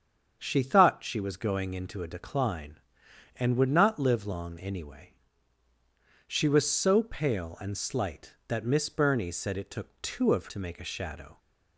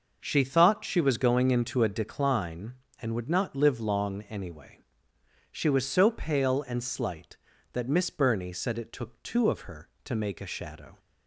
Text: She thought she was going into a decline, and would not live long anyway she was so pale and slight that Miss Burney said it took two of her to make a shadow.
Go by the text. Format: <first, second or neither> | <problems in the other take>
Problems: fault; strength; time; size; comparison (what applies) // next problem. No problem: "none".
second | starts louder than the rest; until 1.4 s; 7 dB // pauses between "anyway" and "she"; strong; at 5.0 s; 1.2 s long; noticeable in the second // skips "her"; at 10.4 s